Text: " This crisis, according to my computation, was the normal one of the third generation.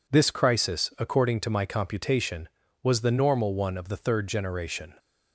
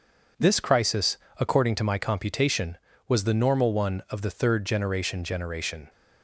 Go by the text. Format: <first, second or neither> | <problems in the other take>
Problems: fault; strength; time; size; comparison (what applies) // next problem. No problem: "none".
first | says "generation" twice; at 5.2 s